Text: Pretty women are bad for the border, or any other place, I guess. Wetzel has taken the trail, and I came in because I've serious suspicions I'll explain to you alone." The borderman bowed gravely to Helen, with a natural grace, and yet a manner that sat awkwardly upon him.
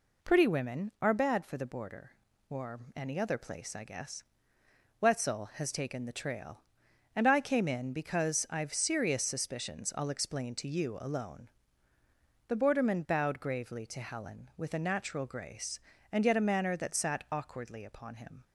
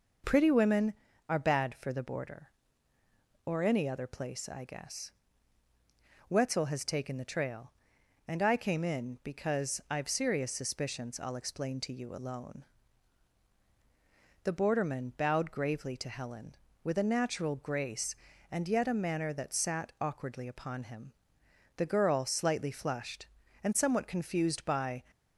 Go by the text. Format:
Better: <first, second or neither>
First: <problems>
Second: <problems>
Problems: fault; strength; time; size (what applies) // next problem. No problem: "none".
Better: first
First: none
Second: goes on to say "The girl slightly flushed and somewhat confused by"; strong; from 21.7 s on; 3.2 s long